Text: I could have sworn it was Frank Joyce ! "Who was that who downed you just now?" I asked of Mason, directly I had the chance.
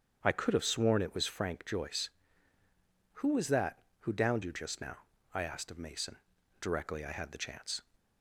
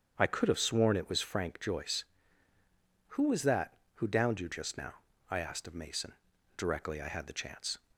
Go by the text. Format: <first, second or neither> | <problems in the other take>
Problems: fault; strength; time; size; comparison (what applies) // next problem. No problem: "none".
neither | starts louder than the rest; strong; the same in both